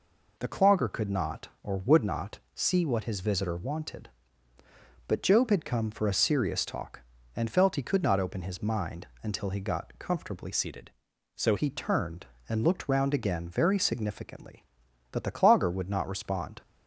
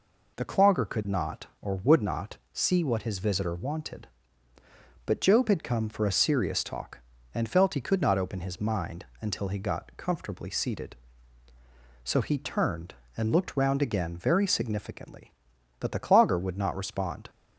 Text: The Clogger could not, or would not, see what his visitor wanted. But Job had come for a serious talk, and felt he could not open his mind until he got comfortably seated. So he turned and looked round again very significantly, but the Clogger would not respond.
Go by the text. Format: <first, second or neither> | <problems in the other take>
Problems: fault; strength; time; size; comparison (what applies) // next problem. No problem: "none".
second | pauses between "mind" and "until"; slight; at 9.0 s; 0.16 s long; slight in the second // changes voice from "seated" to "So"; from 10.5 to 11.5 s; 1.0 s long